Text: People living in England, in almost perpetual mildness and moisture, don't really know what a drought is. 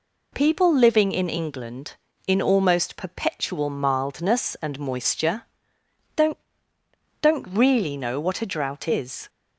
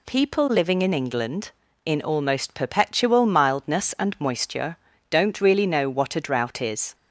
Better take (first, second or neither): second